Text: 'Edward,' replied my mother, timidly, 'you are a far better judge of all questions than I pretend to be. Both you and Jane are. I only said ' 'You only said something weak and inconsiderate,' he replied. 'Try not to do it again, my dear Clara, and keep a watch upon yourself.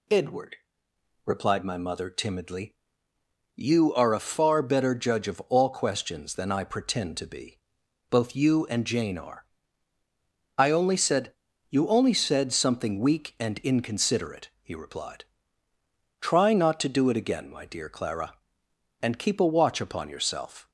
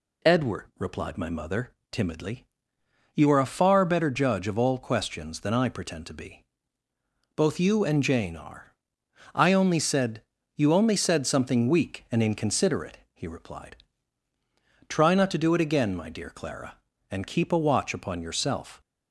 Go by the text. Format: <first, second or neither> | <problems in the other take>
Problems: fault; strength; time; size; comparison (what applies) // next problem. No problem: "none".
neither | none